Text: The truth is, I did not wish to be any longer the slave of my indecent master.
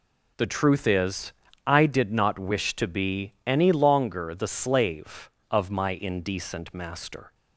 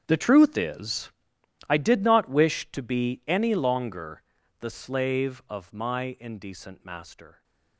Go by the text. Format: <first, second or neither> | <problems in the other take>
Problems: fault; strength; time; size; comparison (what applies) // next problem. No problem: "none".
first | gets quieter; strong; throughout; 17 dB // pauses between "longer" and "the"; at 4.2 s; 0.38 s long